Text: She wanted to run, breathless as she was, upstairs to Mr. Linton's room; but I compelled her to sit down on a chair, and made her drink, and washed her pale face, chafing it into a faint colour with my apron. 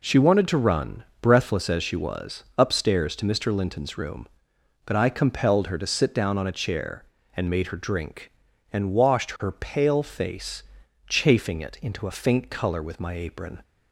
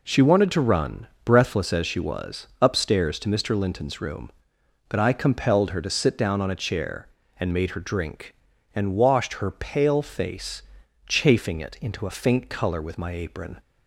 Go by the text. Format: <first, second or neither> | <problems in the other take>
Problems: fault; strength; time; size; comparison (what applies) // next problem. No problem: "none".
neither | none